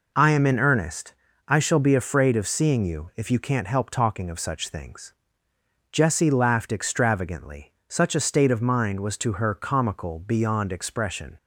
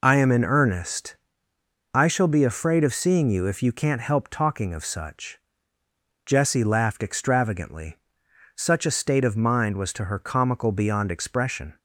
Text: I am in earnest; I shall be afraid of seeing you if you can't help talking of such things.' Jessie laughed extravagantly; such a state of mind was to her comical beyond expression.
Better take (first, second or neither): first